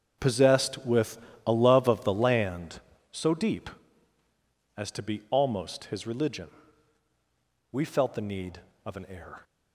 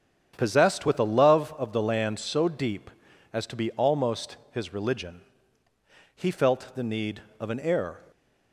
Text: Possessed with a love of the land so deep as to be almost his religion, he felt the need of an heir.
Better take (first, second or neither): second